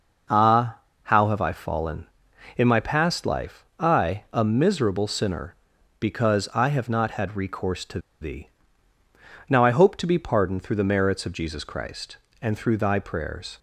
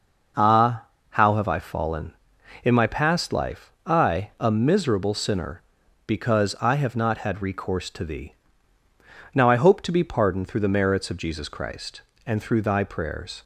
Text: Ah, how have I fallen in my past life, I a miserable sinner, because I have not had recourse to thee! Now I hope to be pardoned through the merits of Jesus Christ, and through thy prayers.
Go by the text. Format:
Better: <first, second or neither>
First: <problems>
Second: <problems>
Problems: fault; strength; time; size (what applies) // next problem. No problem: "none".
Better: second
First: pauses between "to" and "thee"; slight; at 7.9 s; 0.22 s long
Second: none